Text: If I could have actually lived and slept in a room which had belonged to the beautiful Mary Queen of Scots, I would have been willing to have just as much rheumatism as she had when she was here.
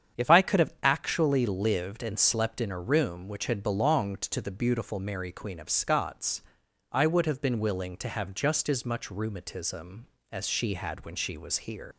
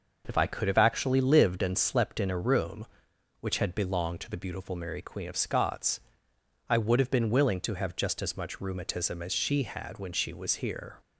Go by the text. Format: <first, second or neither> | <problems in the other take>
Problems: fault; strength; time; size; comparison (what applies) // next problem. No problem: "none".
second | starts louder than the rest; strong; until 1.2 s; 8 dB // leaves "here" unfinished; at 11.9 s; 90 ms